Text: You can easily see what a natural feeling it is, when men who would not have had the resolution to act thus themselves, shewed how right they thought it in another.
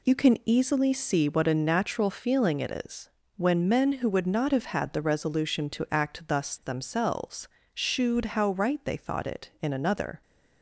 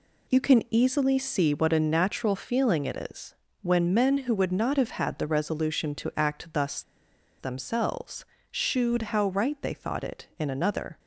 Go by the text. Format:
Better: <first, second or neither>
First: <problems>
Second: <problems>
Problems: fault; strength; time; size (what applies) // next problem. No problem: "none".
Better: first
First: none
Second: pauses between "thus" and "themselves"; noticeable; at 6.8 s; 0.57 s long